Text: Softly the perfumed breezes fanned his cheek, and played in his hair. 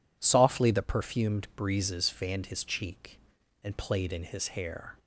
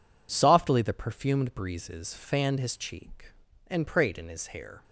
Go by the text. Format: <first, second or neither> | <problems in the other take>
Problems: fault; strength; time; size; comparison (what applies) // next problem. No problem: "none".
first | says "prayed" for "played"; at 3.8 s